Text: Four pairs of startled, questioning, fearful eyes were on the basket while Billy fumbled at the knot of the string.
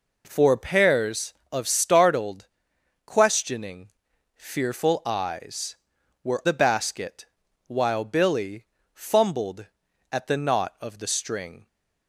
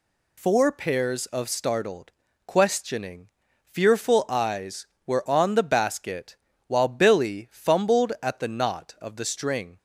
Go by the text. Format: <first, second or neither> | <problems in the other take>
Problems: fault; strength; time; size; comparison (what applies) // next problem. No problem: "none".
second | skips "on"; at 6.4 s // pauses between "basket" and "while"; at 7.2 s; 0.42 s long; slight in the second // pauses between "Billy" and "fumbled"; slight; at 8.6 s; 0.30 s long